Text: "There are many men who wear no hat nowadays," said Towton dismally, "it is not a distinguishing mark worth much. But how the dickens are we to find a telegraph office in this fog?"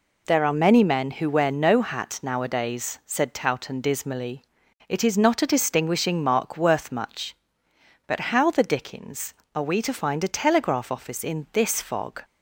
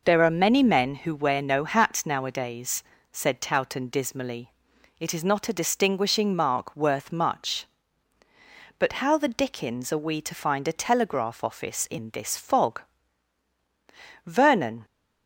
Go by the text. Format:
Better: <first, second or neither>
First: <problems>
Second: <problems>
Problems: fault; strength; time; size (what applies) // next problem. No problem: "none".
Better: first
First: none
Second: goes on to say "Vernon"; from 14.2 s on; 0.58 s long